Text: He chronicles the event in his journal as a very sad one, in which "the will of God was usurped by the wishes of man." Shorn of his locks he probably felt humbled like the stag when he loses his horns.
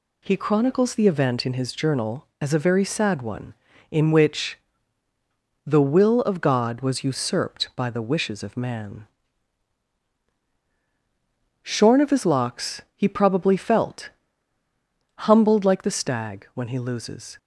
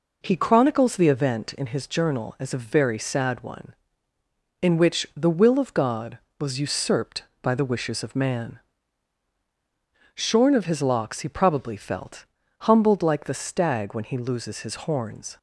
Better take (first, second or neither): second